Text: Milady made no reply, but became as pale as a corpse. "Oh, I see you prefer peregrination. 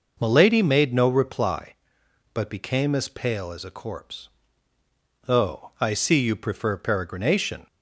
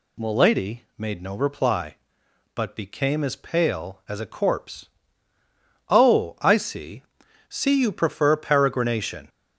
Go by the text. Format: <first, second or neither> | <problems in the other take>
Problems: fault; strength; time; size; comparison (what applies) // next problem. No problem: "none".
first | says "see" twice; at 7.4 s